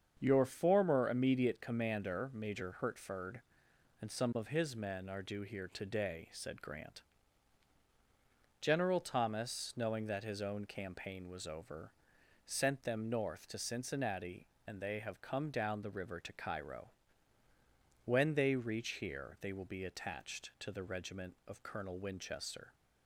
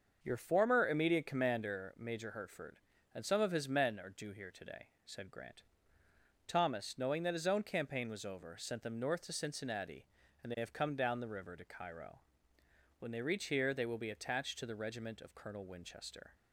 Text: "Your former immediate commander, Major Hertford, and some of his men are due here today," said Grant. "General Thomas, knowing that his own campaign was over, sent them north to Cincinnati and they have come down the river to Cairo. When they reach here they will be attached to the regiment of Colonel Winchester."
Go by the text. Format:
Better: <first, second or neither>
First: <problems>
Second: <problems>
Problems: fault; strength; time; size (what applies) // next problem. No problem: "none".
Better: first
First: starts louder than the rest; until 1.2 s; 7 dB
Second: starts louder than the rest; until 1.2 s; 6.5 dB // skips "General"; at 6.0 s